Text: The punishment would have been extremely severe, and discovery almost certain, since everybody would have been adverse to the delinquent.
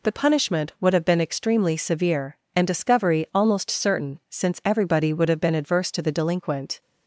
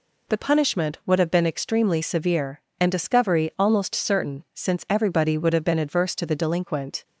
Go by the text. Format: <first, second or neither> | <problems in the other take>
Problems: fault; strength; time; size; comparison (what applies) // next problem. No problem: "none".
neither | none